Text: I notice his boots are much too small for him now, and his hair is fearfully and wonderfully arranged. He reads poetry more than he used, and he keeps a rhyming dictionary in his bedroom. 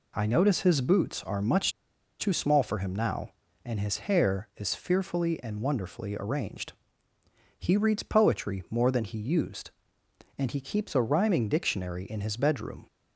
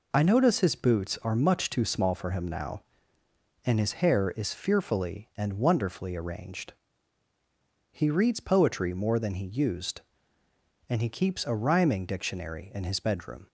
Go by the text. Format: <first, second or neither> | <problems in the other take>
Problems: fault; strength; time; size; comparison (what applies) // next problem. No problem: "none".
second | pauses between "much" and "too"; noticeable; at 1.7 s; 0.48 s long